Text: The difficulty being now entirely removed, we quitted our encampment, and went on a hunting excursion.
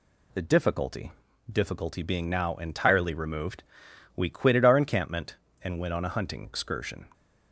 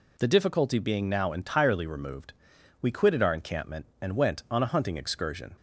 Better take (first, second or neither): second